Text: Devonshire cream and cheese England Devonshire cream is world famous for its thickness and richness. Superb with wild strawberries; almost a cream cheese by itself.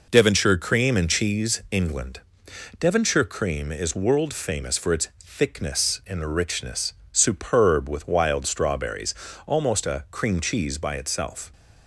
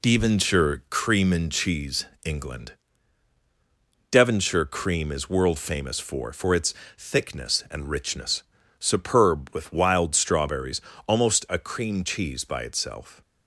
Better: first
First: pauses between "England" and "Devonshire"; noticeable; at 2.2 s; 0.58 s long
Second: pauses between "cheese" and "England"; slight; at 2.0 s; 0.18 s long // pauses between "England" and "Devonshire"; strong; at 2.7 s; 1.3 s long // says "for" twice; at 6.3 s // pauses between "its" and "thickness"; slight; at 6.7 s; 0.24 s long

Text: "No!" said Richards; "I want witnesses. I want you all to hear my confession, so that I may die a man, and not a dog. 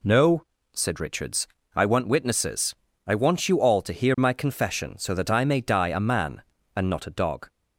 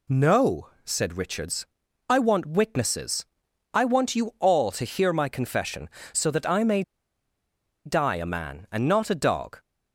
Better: first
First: none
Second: pauses between "may" and "die"; at 6.8 s; 1.0 s long

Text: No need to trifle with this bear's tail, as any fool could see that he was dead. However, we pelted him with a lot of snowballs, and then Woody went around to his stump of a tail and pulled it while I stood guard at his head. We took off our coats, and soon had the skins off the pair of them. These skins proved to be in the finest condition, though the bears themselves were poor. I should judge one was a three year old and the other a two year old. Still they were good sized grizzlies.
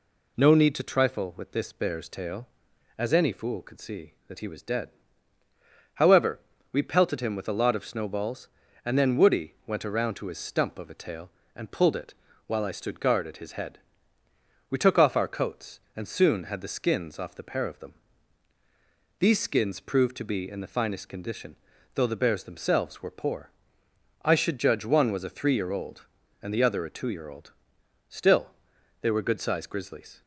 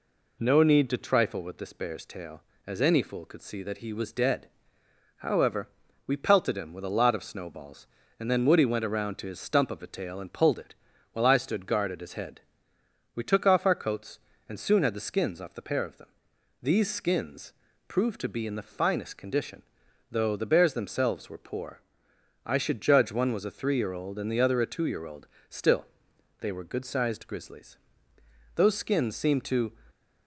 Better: first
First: pauses between "it" and "while"; slight; at 12.1 s; 0.32 s long // pauses between "Still" and "they"; noticeable; at 28.4 s; 0.54 s long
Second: pauses between "it" and "while"; slight; at 10.7 s; 0.36 s long // pauses between "skins" and "proved"; at 17.5 s; 0.38 s long // pauses between "Still" and "they"; noticeable; at 25.8 s; 0.54 s long // goes on to say "Those skins seemed to"; noticeable; from 28.5 s on; 1.1 s long

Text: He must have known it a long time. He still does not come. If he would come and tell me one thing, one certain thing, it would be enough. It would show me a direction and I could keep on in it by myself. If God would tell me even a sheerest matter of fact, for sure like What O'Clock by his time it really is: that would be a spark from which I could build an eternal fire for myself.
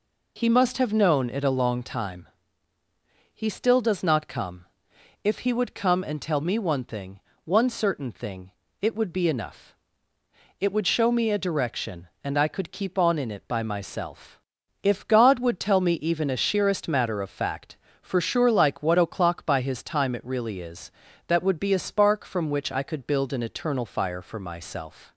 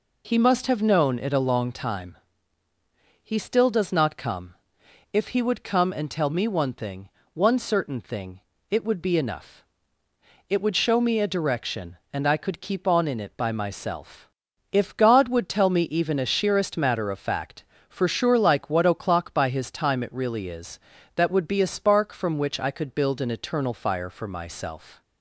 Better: neither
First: none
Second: none

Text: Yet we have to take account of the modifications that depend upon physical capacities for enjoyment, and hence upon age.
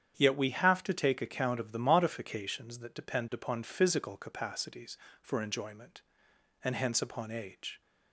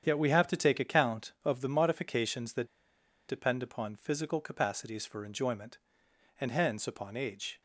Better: first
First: starts louder than the rest; strong; until 1.1 s; 9 dB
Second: starts louder than the rest; strong; until 1.0 s; 8.5 dB // pauses between "that" and "depend"; noticeable; at 2.6 s; 0.62 s long

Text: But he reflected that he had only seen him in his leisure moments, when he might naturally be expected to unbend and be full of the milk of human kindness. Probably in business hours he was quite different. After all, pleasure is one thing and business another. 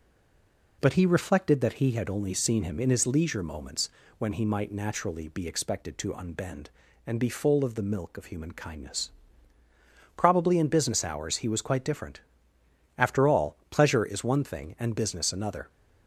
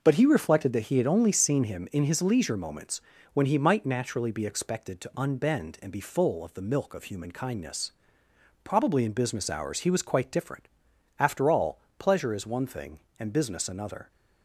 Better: second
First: stays silent before the first word; slight; until 0.7 s; 0.7 s long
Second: none

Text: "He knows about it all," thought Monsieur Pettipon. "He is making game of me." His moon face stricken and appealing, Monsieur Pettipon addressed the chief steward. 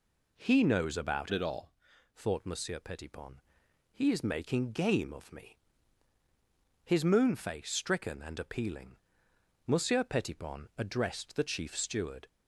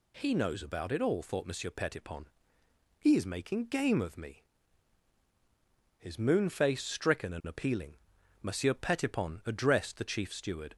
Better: second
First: changes voice from "it" to "all"; from 1.3 to 1.7 s; 0.4 s long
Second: none

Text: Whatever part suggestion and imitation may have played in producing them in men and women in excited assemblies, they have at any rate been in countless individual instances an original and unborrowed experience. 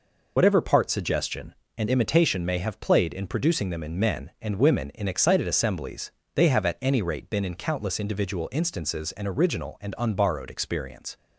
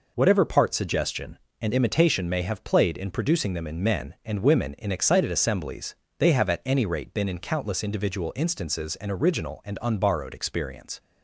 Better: second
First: loses the start of "Whatever"; at 0.3 s; 45 ms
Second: none

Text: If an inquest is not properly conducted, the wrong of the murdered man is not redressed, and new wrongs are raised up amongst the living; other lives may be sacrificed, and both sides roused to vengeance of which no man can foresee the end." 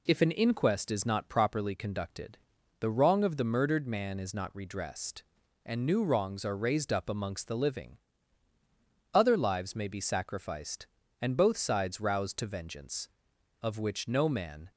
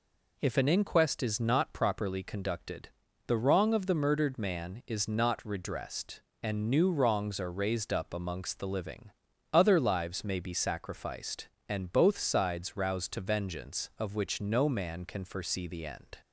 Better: second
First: stops before "can foresee the end"; at 14.7 s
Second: none

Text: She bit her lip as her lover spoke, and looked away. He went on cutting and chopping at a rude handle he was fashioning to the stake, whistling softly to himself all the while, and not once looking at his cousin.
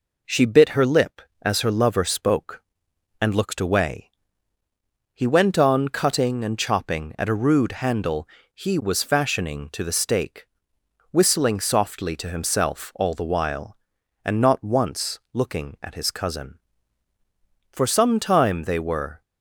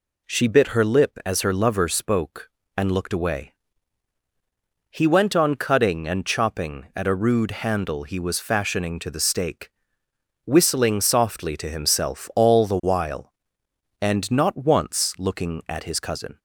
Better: second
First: pauses between "handle" and "he"; slight; at 8.2 s; 0.24 s long // goes on to say "For some time they were"; from 17.7 s on; 1.5 s long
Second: none

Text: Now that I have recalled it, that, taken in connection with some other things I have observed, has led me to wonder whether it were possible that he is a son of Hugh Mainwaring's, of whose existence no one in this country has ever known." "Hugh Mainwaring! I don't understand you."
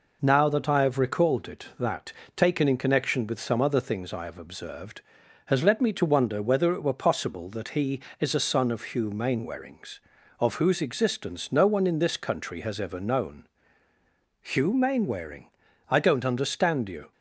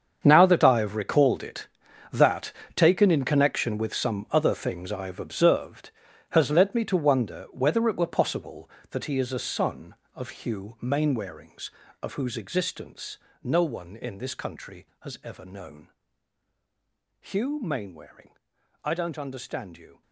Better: first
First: none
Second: gets quieter; strong; throughout; 15.5 dB // pauses between "existence" and "no"; slight; at 13.1 s; 0.26 s long

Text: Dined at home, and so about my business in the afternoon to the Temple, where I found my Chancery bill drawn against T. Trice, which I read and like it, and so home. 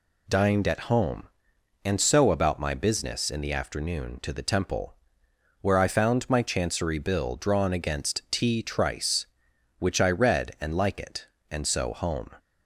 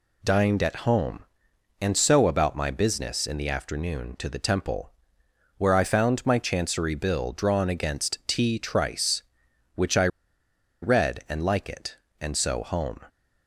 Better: first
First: none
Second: pauses between "I" and "read"; noticeable; at 10.0 s; 0.74 s long

